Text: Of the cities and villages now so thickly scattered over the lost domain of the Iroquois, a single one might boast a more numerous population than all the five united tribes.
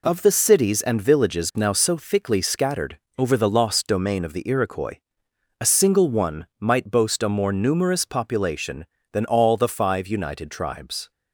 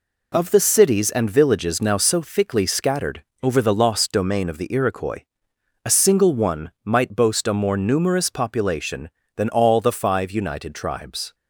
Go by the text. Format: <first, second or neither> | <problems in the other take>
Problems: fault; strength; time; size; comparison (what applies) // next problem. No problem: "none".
neither | pauses between "scattered" and "over"; slight; the same in both